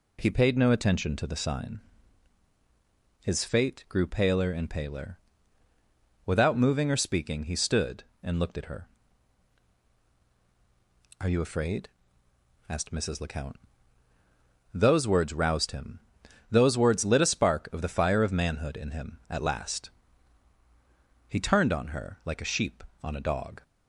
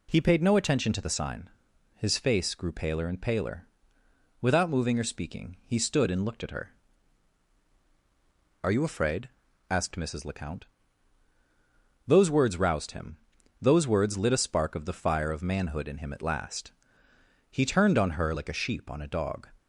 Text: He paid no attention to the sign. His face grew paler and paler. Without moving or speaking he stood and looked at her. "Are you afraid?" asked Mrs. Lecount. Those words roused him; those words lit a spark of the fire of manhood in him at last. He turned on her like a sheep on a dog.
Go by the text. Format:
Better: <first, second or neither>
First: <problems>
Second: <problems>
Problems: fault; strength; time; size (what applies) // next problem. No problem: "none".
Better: second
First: says "fate" for "face"; at 3.4 s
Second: none